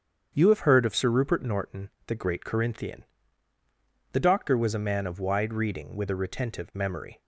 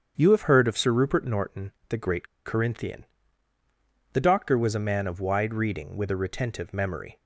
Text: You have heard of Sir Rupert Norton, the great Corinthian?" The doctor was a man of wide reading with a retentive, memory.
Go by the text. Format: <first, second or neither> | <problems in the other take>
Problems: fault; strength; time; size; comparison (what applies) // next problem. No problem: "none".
first | starts louder than the rest; strong; until 1.1 s; 8 dB; strong in the first // pauses between "great" and "Corinthian"; slight; at 2.2 s; 0.20 s long